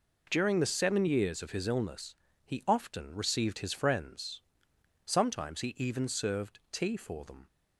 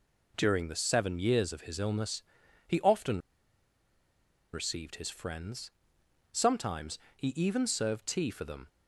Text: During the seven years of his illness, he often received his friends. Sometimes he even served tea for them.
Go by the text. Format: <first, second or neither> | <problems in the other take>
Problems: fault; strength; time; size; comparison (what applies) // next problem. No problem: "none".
first | pauses between "often" and "received"; strong; at 3.1 s; 1.3 s long // pauses between "Sometimes" and "he"; slight; at 6.9 s; 0.18 s long